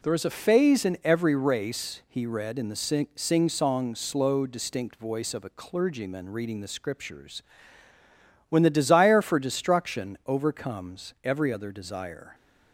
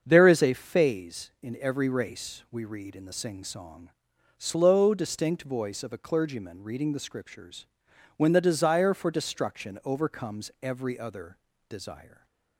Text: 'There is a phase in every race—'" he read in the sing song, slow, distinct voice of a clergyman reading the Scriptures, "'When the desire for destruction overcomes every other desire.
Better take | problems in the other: first | starts louder than the rest; until 1.0 s; 7 dB // says "we" for "he"; at 2.5 s // pauses between "other" and "desire"; slight; at 11.3 s; 0.32 s long

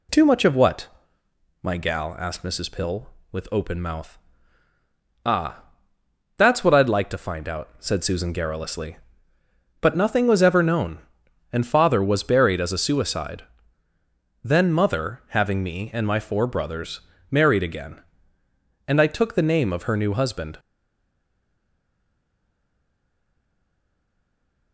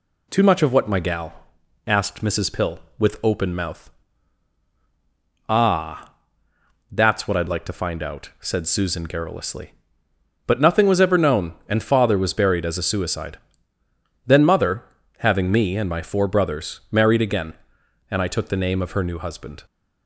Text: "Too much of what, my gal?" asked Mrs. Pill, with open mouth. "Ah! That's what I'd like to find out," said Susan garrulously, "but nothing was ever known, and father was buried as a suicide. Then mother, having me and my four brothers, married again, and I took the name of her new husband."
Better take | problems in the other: second | stays silent after the last word; strong; from 20.5 s on; 4.2 s long

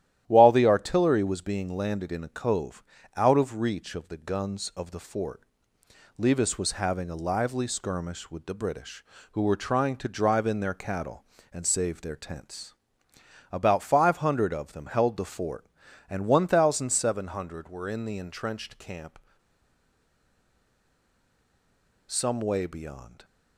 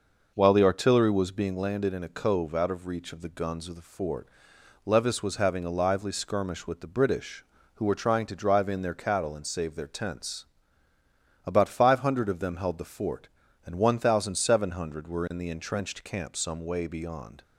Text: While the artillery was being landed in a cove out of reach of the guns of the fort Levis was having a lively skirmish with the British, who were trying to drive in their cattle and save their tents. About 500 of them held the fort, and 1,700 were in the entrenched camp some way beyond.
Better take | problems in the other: second | starts louder than the rest; strong; until 1.2 s; 12.5 dB // pauses between "cove" and "out"; slight; at 2.8 s; 0.32 s long // pauses between "fort" and "Levis"; noticeable; at 5.4 s; 0.76 s long; noticeable in the second // pauses between "camp" and "some"; strong; at 19.1 s; 2.8 s long

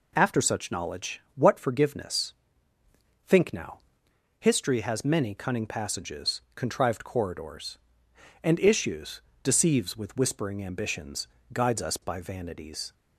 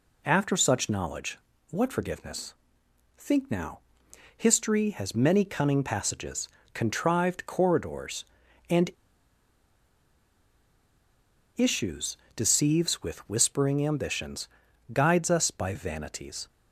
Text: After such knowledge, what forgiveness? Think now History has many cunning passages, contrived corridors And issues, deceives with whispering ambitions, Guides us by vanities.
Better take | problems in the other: first | pauses between "now" and "History"; noticeable; at 3.7 s; 0.58 s long; noticeable in the first // pauses between "And" and "issues"; strong; at 8.9 s; 2.6 s long

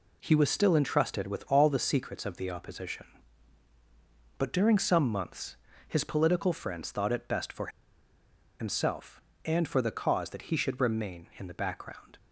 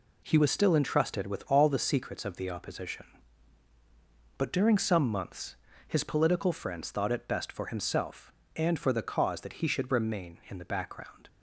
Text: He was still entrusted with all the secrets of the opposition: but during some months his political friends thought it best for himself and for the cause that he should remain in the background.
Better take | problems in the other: second | pauses between "months" and "his"; slight; at 5.5 s; 0.32 s long; slight in the second // pauses between "for" and "himself"; noticeable; at 7.6 s; 0.91 s long

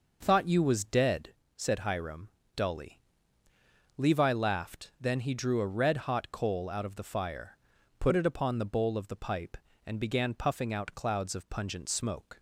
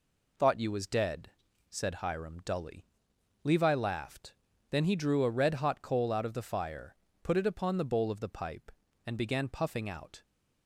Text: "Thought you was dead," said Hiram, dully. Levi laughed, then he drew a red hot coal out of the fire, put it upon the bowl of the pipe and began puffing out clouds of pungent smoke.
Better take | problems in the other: first | stops before "clouds of pungent smoke"; at 10.2 s

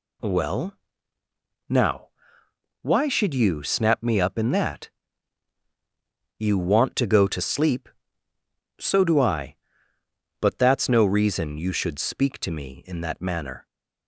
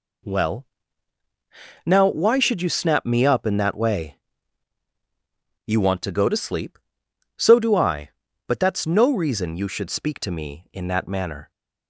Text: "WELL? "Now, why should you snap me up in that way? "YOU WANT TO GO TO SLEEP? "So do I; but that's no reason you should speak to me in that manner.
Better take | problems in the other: second | skips "way"; at 5.6 s

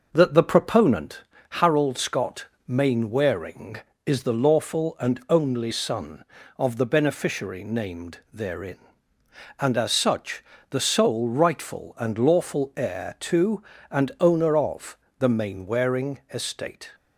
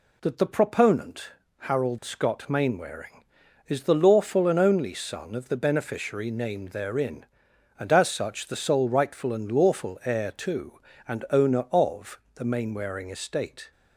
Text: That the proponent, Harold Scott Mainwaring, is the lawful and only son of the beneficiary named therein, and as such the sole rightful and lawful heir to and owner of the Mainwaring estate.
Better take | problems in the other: second | starts louder than the rest; noticeable; until 1.1 s; 5.5 dB // pauses between "Scott" and "Mainwaring"; slight; at 2.4 s; 0.20 s long // pauses between "such" and "the"; slight; at 10.4 s; 0.28 s long // pauses between "of" and "the"; slight; at 14.9 s; 0.24 s long; slight in the second

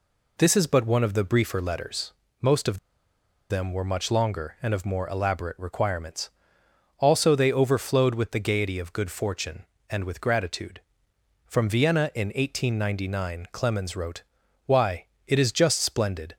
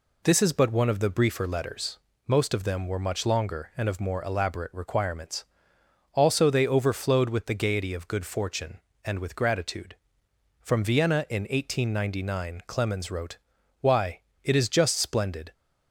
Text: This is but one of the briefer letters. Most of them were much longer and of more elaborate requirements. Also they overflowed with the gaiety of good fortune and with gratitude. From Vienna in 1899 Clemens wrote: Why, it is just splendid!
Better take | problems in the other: second | pauses between "of" and "them"; noticeable; at 2.7 s; 0.73 s long

